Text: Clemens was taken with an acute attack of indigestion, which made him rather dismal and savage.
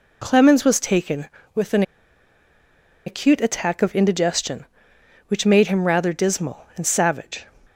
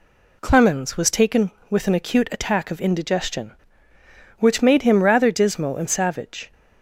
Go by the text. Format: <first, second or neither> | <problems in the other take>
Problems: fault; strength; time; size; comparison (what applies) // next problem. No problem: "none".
second | pauses between "an" and "acute"; at 1.8 s; 1.2 s long